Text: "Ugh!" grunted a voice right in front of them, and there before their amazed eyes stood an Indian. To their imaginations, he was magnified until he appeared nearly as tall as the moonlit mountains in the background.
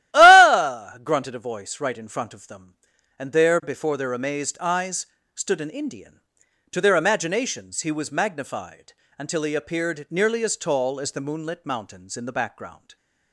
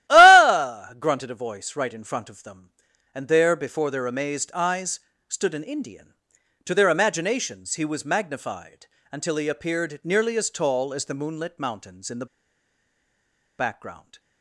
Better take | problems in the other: first | starts louder than the rest; strong; until 1.1 s; 14 dB; strong in the first // pauses between "eyes" and "stood"; slight; at 4.9 s; 0.30 s long; slight in the first // pauses between "magnified" and "until"; slight; at 8.8 s; 0.26 s long; slight in the first // pauses between "the" and "background"; strong; at 12.2 s; 1.3 s long

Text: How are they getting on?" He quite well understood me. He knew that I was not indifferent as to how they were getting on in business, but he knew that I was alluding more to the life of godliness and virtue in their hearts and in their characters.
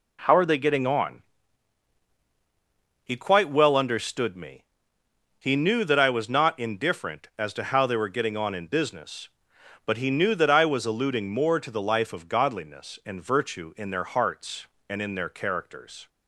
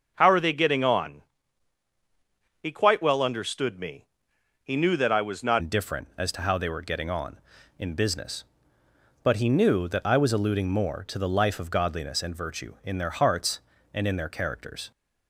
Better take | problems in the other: first | starts louder than the rest; noticeable; until 1.1 s; 6 dB // changes voice at "indifferent"; from 5.5 s on; 9.4 s long

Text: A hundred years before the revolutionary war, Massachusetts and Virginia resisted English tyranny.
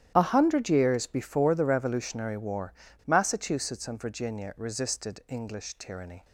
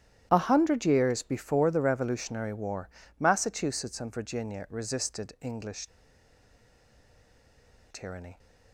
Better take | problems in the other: first | starts louder than the rest; strong; until 1.3 s; 11.5 dB; strong in the first // pauses between "English" and "tyranny"; strong; at 5.8 s; 2.0 s long

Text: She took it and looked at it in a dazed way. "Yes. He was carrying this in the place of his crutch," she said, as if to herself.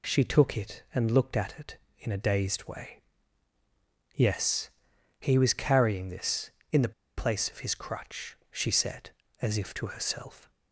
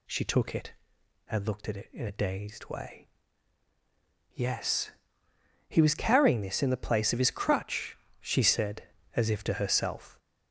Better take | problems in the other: second | pauses between "the" and "place"; slight; at 6.9 s; 0.26 s long

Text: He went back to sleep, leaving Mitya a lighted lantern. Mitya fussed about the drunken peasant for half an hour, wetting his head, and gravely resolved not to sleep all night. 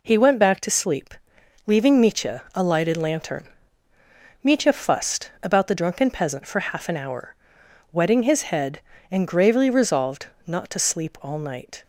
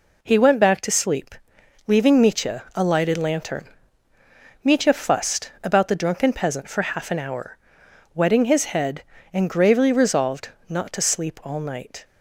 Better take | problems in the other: neither | pauses between "resolved" and "not"; slight; the same in both

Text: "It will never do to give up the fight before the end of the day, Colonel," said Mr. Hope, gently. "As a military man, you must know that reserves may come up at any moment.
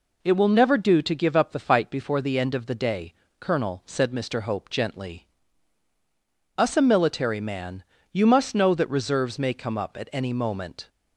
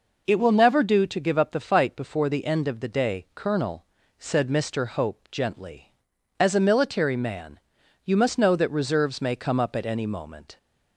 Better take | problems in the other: second | says "Us" for "As"; at 6.5 s

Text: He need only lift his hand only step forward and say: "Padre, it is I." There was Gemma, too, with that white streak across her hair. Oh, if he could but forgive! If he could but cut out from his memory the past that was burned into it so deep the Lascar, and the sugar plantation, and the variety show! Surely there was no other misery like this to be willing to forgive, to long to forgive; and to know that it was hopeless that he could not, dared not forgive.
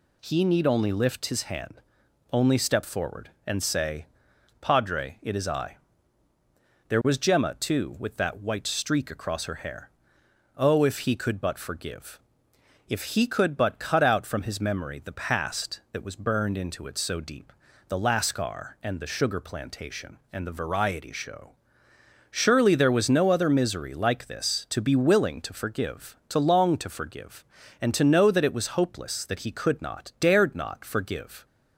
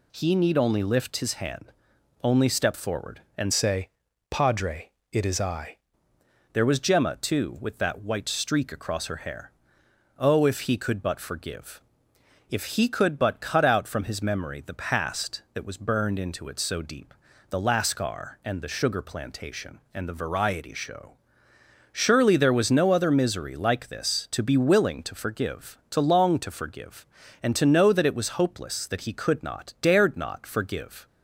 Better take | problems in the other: first | pauses between "hand" and "only"; noticeable; at 1.6 s; 0.58 s long; noticeable in the first // changes voice from "say" to "I"; from 3.5 to 5.7 s; 2.2 s long // pauses between "deep" and "the"; slight; at 17.1 s; 0.36 s long; slight in the first

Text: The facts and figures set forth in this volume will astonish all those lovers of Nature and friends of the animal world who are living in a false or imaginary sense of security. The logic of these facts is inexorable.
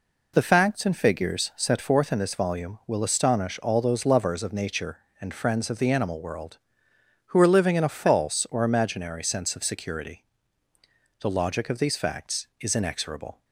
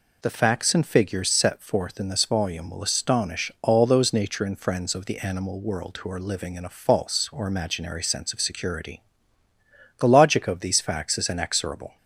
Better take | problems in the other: first | skips "lovers of"; at 4.1 s

